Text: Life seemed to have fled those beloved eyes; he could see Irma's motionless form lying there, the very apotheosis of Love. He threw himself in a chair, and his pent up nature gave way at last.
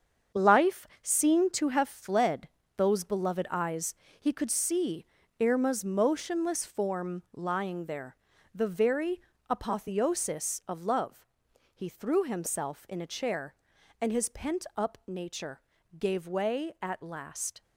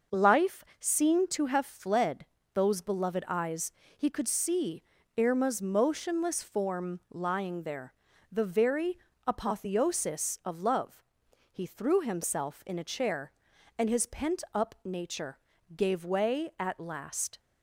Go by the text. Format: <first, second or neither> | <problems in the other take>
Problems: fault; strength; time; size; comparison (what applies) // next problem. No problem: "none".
second | gets quieter; strong; throughout; 8.5 dB // starts louder than the rest; strong; until 1.5 s; 7 dB; noticeable in the second // pauses between "Life" and "seemed"; slight; at 0.8 s; 0.16 s long; slight in the second // pauses between "fled" and "those"; slight; at 2.4 s; 0.28 s long; slight in the second // pauses between "see" and "Irma's"; slight; at 5.0 s; 0.34 s long; slight in the second // pauses between "very" and "apotheosis"; slight; at 9.2 s; 0.30 s long; slight in the second // pauses between "nature" and "gave"; at 15.6 s; 0.38 s long; also in the second